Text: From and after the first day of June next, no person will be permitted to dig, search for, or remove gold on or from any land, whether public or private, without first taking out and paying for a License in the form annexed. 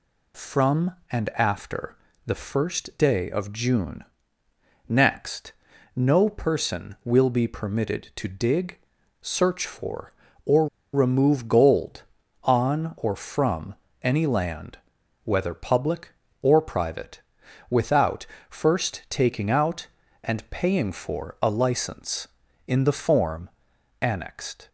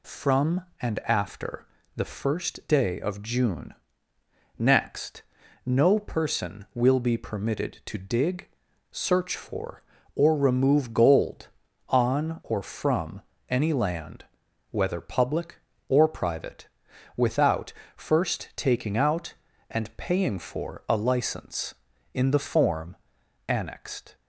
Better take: second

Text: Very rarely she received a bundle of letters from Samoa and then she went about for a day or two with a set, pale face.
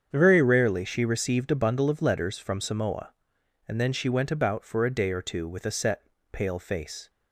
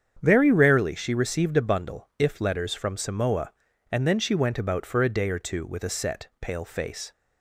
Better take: first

